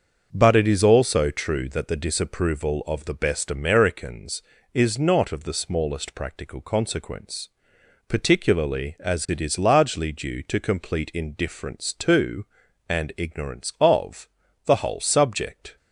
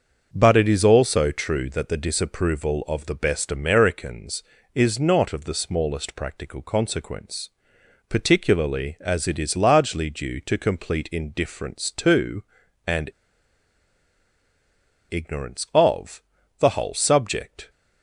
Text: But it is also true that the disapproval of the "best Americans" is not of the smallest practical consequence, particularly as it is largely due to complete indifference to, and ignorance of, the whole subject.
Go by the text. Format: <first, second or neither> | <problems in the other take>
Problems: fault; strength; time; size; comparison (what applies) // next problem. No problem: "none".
first | starts louder than the rest; until 1.3 s; 6.5 dB; also in the first // pauses between "and" and "ignorance"; strong; at 13.0 s; 1.9 s long